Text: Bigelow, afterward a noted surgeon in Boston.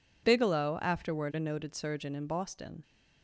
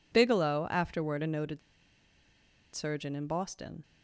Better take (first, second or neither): first